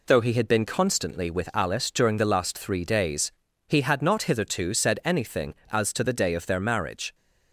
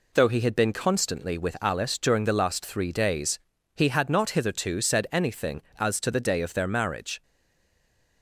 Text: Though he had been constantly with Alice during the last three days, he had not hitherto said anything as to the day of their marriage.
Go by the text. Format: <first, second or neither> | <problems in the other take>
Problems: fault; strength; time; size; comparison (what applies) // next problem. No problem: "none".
first | stays silent after the last word; from 7.2 s on; 1.0 s long